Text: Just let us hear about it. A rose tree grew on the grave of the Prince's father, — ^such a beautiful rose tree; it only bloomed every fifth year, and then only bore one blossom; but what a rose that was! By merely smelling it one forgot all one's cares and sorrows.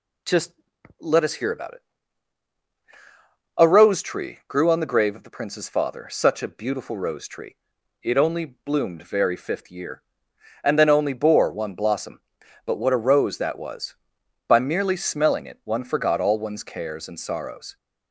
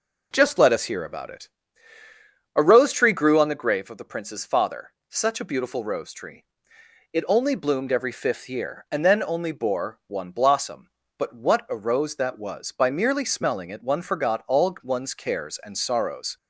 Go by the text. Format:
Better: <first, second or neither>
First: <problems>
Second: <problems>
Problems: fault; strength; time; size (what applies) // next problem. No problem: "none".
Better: second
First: pauses between "Just" and "let"; noticeable; at 0.5 s; 0.46 s long // says "very" for "every"; at 9.0 s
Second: none